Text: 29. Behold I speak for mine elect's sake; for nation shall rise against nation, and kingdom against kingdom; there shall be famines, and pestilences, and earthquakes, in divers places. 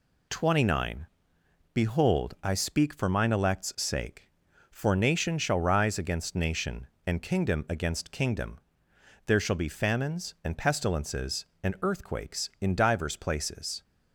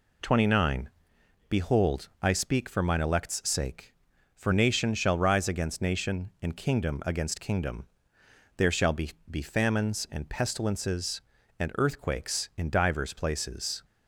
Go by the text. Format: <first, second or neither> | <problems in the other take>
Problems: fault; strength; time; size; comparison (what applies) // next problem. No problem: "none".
first | says "be" twice; at 9.3 s